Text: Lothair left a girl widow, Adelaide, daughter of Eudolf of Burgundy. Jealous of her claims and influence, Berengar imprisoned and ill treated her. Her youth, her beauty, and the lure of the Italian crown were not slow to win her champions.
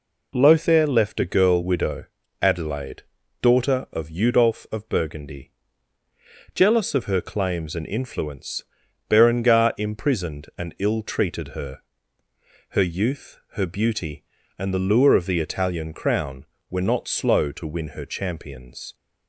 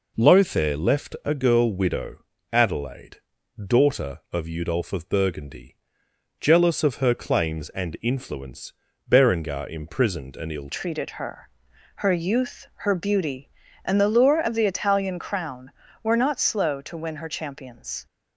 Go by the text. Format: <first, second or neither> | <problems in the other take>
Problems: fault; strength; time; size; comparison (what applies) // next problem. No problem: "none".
first | changes voice at "treated"; from 10.7 s on; 7.3 s long